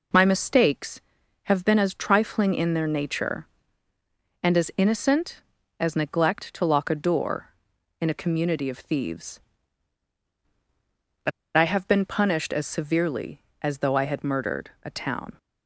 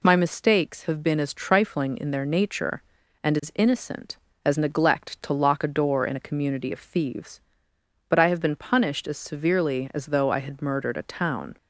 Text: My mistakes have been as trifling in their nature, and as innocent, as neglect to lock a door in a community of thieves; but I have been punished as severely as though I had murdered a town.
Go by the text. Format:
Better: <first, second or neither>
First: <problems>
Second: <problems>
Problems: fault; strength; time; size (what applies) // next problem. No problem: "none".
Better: second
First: pauses between "but" and "I"; slight; at 11.3 s; 0.24 s long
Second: none